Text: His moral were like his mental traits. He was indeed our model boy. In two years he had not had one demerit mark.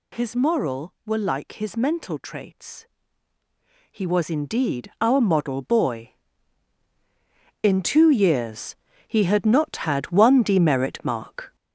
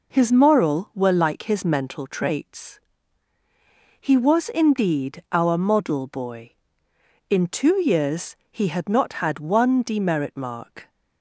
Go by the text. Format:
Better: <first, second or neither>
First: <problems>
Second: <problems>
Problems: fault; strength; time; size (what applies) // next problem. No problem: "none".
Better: second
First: gets louder; noticeable; throughout; 5.5 dB // pauses between "years" and "he"; slight; at 8.7 s; 0.32 s long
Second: pauses between "years" and "he"; slight; at 8.3 s; 0.16 s long